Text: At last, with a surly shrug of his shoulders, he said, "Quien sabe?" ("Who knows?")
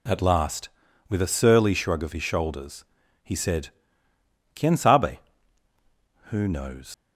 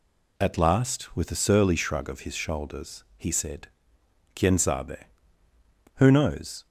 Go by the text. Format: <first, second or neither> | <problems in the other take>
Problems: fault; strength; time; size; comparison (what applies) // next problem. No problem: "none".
second | leaves "knows" unfinished; at 6.9 s; 65 ms